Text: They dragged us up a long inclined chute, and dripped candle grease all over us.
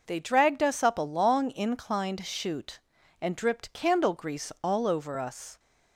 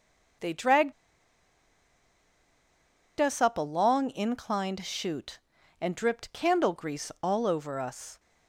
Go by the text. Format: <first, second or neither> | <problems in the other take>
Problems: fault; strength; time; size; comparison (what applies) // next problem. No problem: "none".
first | pauses between "dragged" and "us"; strong; at 0.9 s; 2.2 s long